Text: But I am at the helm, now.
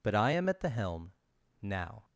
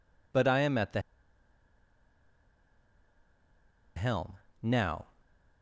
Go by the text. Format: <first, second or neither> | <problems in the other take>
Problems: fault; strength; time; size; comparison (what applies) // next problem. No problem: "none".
first | pauses between "the" and "helm"; strong; at 0.9 s; 2.9 s long